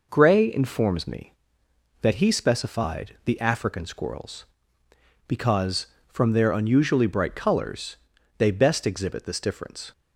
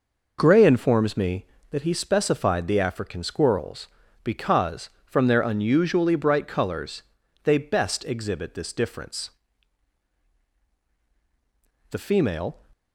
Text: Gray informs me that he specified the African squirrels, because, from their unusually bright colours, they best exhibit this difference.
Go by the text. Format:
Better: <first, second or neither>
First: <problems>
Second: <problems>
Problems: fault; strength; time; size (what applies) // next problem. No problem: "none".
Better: first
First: none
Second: goes on to say "The female"; noticeable; from 11.8 s on; 0.70 s long